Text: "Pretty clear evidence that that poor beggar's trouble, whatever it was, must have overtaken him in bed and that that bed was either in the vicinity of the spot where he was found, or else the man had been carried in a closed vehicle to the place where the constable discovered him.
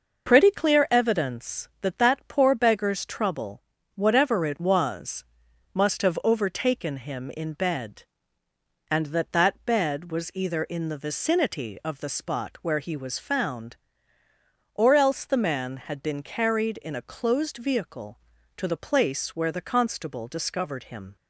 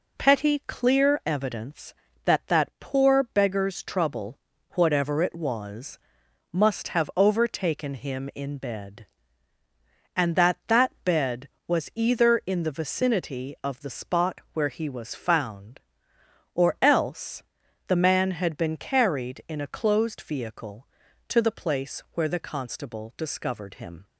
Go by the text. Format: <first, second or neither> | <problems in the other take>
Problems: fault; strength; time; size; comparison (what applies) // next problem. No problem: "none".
first | says "Petty" for "Pretty"; at 0.1 s // pauses between "else" and "the"; noticeable; at 17.4 s; 0.46 s long